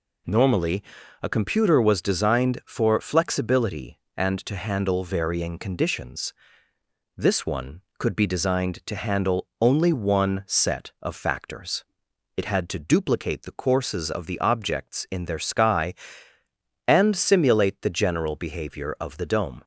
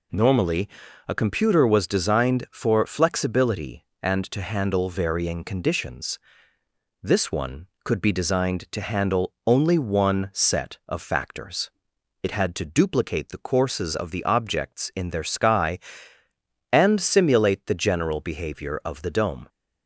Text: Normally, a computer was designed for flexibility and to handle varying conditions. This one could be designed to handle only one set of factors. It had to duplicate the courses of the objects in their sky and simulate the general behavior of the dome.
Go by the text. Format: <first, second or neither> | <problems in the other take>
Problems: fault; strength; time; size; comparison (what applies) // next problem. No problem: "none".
neither | none